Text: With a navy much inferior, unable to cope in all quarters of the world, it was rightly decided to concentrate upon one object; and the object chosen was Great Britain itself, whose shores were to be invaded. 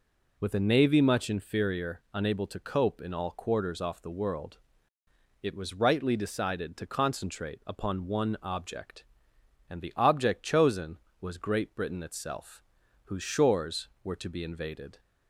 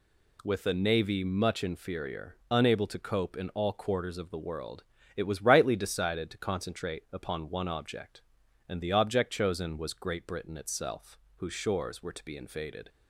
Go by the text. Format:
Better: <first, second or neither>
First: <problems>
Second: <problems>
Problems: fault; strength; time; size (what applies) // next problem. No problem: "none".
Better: second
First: says "off" for "of"; at 3.8 s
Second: none